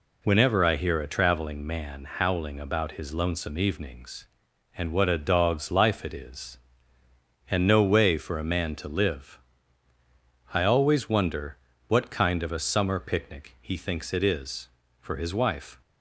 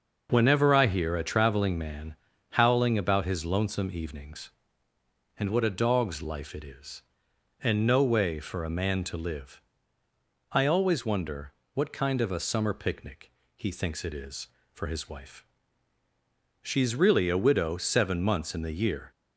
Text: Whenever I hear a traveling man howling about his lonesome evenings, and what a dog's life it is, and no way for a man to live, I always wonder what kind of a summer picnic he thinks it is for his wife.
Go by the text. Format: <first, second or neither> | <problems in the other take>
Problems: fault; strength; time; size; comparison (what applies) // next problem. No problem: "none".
first | starts louder than the rest; noticeable; until 1.3 s; 6 dB // pauses between "man" and "howling"; slight; at 2.1 s; 0.36 s long // pauses between "wonder" and "what"; slight; at 11.5 s; 0.24 s long; slight in the first // pauses between "picnic" and "he"; slight; at 13.3 s; 0.24 s long // goes on to say "She's really a widow seven months in the year"; strong; from 16.6 s on; 2.4 s long